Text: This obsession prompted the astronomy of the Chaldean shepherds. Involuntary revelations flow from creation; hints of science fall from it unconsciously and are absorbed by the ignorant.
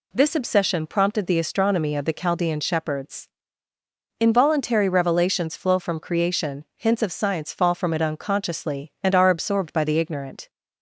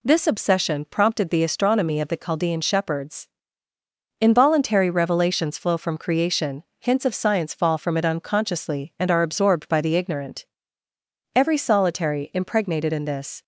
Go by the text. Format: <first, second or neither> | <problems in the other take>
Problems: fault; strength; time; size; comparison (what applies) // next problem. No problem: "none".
first | goes on to say "Every solitary impregnated in this"; strong; from 11.3 s on; 2.0 s long